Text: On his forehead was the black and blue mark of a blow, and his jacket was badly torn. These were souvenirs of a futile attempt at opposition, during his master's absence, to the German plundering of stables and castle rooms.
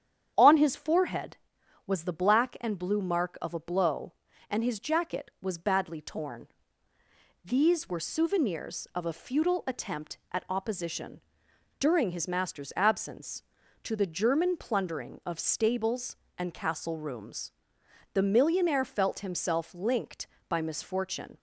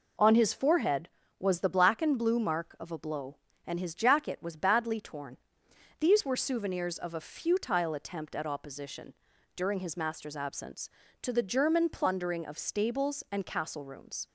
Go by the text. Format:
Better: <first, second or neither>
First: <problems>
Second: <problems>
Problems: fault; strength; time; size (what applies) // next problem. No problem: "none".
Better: second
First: starts louder than the rest; strong; until 1.3 s; 9 dB // goes on to say "The millionaire felt himself linked by misfortune"; strong; from 18.1 s on; 3.2 s long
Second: none